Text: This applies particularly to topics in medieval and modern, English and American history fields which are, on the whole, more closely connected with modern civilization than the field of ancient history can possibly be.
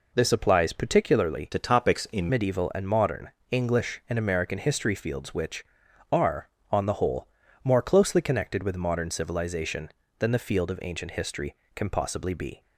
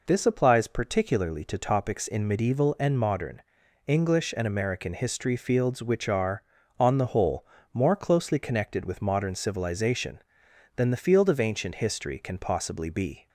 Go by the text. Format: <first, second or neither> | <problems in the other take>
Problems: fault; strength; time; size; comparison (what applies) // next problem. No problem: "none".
second | changes voice from "to" to "in"; from 1.5 to 2.2 s; 0.7 s long